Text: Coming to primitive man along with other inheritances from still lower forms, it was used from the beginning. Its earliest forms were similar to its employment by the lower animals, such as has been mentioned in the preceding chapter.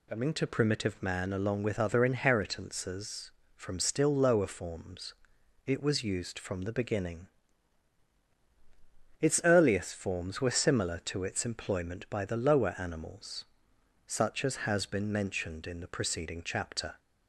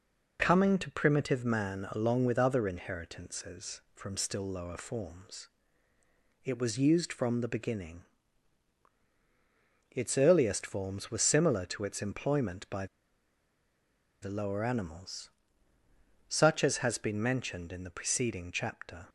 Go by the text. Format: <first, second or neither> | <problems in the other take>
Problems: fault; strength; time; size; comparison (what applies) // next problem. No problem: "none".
first | pauses between "by" and "the"; strong; at 12.8 s; 1.3 s long